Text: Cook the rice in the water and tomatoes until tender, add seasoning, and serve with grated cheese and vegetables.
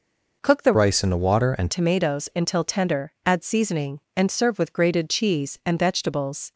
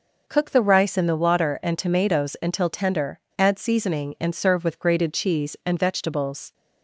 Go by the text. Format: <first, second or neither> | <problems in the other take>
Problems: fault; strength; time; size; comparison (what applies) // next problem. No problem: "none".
second | changes voice from "rice" to "and"; from 0.7 to 1.6 s; 0.9 s long